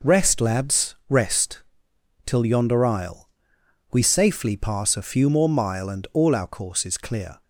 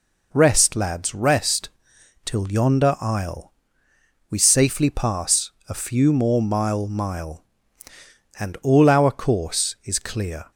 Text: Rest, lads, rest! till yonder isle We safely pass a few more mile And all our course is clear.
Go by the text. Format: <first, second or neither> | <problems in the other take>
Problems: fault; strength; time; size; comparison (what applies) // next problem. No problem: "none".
first | pauses between "isle" and "We"; noticeable; at 3.5 s; 0.78 s long; noticeable in the first // pauses between "pass" and "a"; slight; at 5.5 s; 0.18 s long // says "mile" twice; at 6.8 s